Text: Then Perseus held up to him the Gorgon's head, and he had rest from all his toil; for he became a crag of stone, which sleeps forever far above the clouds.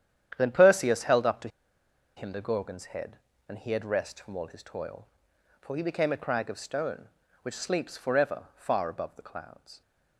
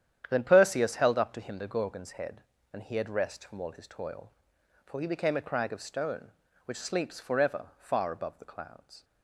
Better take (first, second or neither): second